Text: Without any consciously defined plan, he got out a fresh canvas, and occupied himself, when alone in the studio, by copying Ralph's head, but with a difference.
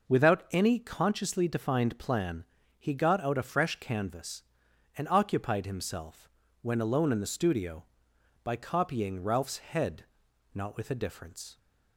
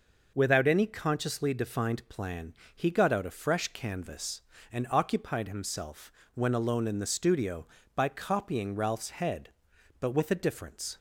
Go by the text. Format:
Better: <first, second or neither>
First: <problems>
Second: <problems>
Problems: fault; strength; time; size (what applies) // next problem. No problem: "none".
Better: second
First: says "not" for "but"; at 10.5 s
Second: none